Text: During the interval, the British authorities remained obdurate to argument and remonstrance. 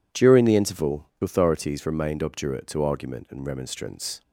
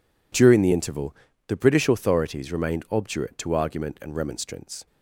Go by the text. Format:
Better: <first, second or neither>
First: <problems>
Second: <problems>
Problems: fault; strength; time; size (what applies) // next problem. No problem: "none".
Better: second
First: skips "the British"; at 1.1 s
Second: none